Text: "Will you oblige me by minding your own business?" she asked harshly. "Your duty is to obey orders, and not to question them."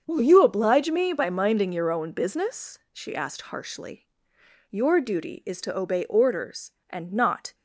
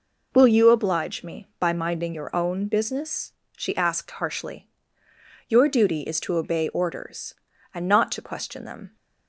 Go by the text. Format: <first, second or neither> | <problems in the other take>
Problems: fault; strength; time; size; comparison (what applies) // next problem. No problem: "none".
second | starts louder than the rest; until 1.0 s; 7 dB // stops before "to question them"; at 7.5 s